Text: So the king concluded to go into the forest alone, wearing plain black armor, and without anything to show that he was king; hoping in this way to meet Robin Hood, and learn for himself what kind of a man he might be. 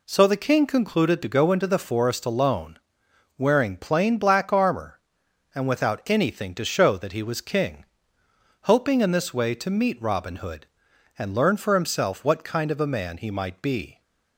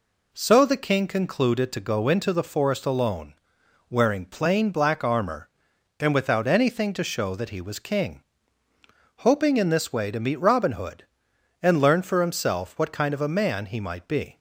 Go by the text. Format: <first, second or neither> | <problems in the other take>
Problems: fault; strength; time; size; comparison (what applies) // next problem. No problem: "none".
neither | none